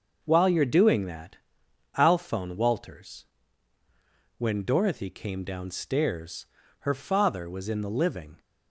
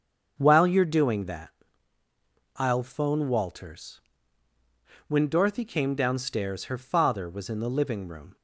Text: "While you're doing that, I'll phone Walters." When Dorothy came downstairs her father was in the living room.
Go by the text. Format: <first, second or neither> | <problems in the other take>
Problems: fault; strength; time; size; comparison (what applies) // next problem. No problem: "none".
second | starts louder than the rest; until 1.2 s; 6.5 dB; also in the second // pauses between "downstairs" and "her"; slight; at 6.4 s; 0.34 s long // stops before "room"; at 8.3 s